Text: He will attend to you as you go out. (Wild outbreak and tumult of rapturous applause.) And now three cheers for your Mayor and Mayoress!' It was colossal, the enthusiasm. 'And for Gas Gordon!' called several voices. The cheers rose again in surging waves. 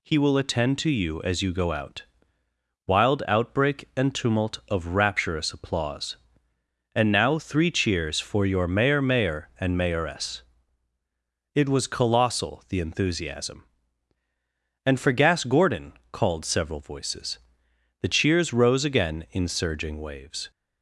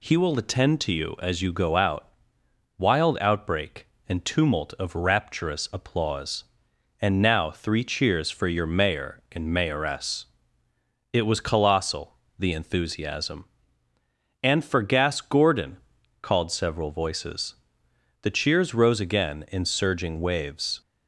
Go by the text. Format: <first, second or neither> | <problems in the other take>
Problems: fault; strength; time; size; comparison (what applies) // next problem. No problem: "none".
second | says "Mayor" twice; at 9.0 s